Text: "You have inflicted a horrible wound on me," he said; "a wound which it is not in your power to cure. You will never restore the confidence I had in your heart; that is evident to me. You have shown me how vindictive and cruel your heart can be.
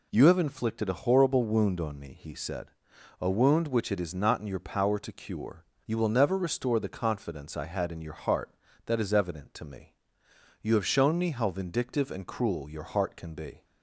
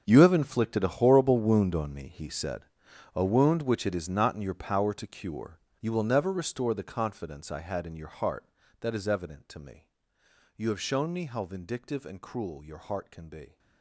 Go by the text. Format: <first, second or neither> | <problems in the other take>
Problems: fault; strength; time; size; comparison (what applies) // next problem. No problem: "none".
first | gets quieter; strong; throughout; 16 dB